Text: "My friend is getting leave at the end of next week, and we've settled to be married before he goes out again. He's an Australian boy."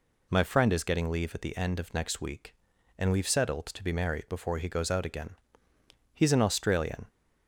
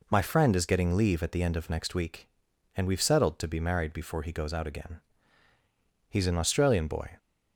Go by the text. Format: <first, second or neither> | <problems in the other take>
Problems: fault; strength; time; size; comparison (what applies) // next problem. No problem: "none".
second | stops before "boy"; at 7.0 s